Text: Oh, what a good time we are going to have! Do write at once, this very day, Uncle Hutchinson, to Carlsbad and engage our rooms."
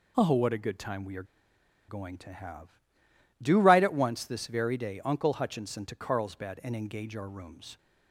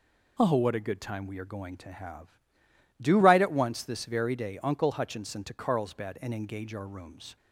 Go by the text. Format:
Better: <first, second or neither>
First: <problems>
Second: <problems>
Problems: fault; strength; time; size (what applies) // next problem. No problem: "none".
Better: second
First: pauses between "are" and "going"; noticeable; at 1.2 s; 0.64 s long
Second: none